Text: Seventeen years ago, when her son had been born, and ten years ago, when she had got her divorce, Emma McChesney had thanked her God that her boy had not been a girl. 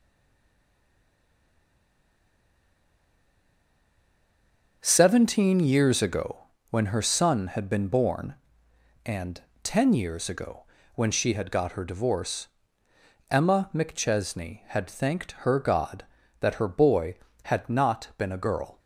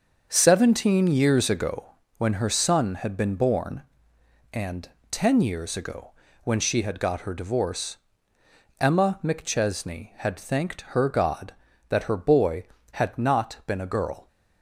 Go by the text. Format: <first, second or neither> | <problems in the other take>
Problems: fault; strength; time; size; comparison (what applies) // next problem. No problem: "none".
second | stays silent before the first word; strong; until 4.8 s; 4.8 s long // starts louder than the rest; until 5.8 s; 6.5 dB; also in the second // pauses between "and" and "ten"; slight; at 9.4 s; 0.20 s long; slight in the second